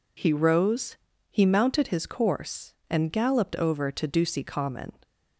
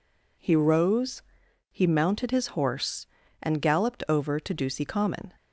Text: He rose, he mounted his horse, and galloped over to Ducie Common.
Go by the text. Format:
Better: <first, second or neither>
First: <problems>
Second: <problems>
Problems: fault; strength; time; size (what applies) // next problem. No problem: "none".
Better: second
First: says "course" for "horse"; at 2.0 s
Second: none